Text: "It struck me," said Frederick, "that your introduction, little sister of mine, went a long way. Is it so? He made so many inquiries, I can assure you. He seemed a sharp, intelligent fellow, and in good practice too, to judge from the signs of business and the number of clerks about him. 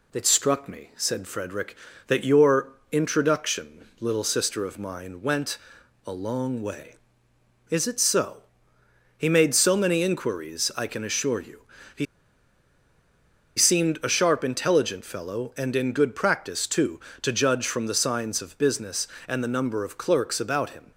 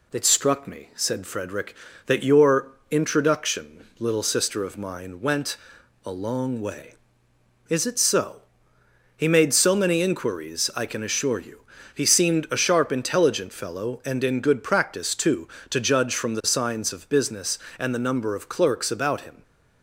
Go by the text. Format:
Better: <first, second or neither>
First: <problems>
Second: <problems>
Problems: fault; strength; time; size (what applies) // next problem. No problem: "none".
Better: second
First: pauses between "your" and "introduction"; slight; at 2.6 s; 0.20 s long // pauses between "went" and "a"; noticeable; at 5.5 s; 0.48 s long // pauses between "He" and "seemed"; strong; at 12.0 s; 1.5 s long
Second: pauses between "your" and "introduction"; slight; at 2.6 s; 0.20 s long // pauses between "went" and "a"; noticeable; at 5.5 s; 0.48 s long